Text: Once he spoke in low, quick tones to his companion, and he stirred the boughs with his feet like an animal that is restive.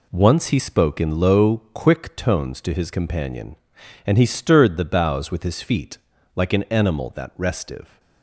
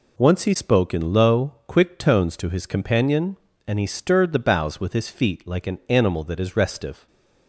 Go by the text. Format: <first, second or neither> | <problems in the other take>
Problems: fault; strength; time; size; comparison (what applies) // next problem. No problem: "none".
second | pauses between "feet" and "like"; at 5.9 s; 0.38 s long // skips "is"; at 7.3 s